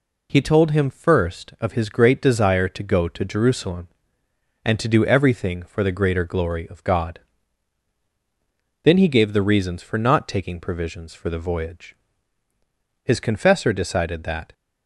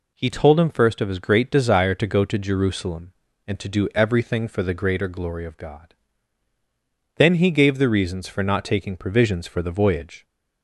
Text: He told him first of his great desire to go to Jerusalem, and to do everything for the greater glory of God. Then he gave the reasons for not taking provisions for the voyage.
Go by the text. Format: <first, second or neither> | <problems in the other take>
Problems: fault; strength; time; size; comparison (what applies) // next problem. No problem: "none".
second | goes on to say "His confessor decided that"; from 13.0 s on; 1.5 s long